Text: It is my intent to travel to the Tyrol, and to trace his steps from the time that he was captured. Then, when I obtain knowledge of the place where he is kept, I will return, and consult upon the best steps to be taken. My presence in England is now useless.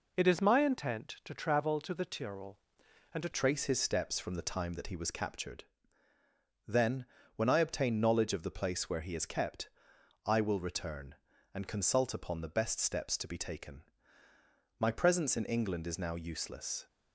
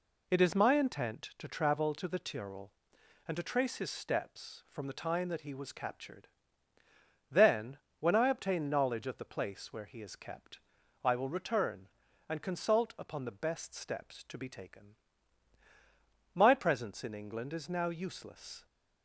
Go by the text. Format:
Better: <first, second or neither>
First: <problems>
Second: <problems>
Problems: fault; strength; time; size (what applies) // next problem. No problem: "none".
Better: second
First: changes voice at "trace"; from 3.3 s on; 13.5 s long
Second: none